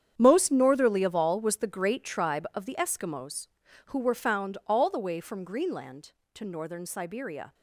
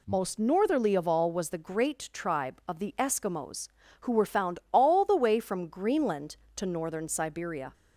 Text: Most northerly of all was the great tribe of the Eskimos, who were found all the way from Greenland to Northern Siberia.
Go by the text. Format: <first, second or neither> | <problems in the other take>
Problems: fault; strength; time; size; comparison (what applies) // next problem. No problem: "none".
second | gets quieter; strong; throughout; 13 dB